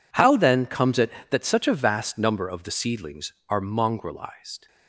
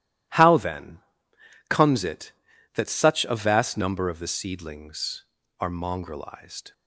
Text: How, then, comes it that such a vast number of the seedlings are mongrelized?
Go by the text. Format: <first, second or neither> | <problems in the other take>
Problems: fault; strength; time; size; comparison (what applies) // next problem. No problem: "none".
neither | none